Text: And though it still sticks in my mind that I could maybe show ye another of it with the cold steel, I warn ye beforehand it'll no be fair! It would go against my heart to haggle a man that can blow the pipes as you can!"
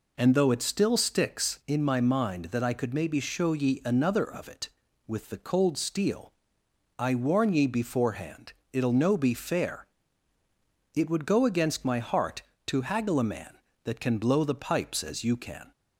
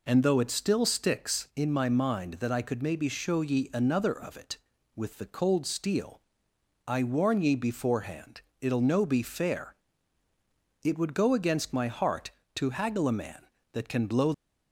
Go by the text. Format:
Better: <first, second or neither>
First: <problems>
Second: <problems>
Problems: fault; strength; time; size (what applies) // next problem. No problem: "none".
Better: first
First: pauses between "beforehand" and "it'll"; slight; at 8.5 s; 0.20 s long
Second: pauses between "beforehand" and "it'll"; slight; at 8.4 s; 0.20 s long // stops before "the pipes as you can"; at 14.3 s